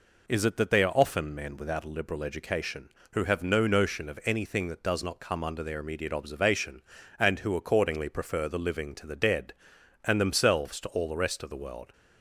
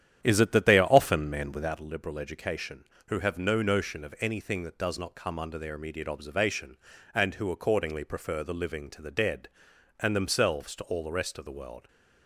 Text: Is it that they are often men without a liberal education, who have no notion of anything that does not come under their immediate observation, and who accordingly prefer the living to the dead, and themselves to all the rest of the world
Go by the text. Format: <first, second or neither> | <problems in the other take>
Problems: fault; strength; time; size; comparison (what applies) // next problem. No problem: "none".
first | starts louder than the rest; strong; until 1.7 s; 10 dB